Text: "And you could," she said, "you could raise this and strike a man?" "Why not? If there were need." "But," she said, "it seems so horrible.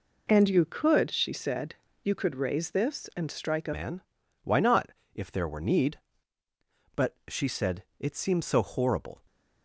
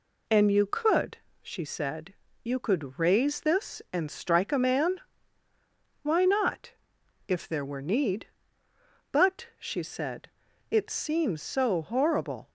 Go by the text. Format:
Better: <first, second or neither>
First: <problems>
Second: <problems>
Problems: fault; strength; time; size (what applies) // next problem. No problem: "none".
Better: second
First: changes voice at "man"; from 3.7 s on; 5.4 s long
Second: none